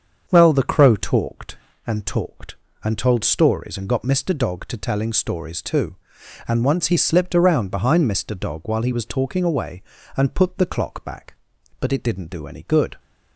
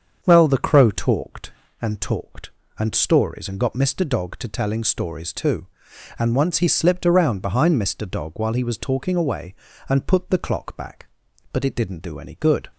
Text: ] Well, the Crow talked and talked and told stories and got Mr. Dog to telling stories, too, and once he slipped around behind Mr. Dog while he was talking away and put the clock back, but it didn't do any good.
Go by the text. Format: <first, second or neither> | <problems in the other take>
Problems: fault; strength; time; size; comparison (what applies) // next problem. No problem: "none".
first | starts louder than the rest; until 1.2 s; 7 dB; also in the first // skips "told"; at 2.9 s